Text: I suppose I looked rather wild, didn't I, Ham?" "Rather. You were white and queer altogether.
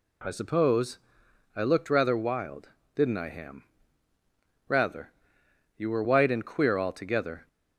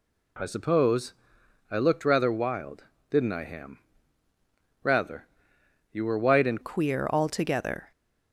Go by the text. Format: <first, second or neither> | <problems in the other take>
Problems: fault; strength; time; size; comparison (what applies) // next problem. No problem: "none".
first | pauses between "suppose" and "I"; noticeable; at 1.1 s; 0.56 s long; noticeable in the first // changes voice at "queer"; from 6.6 s on; 1.3 s long